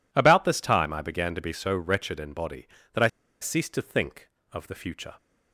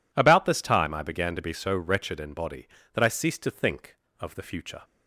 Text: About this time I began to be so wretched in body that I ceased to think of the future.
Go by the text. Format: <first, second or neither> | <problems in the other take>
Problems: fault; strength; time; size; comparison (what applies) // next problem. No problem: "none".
second | pauses between "I" and "ceased"; slight; at 3.0 s; 0.34 s long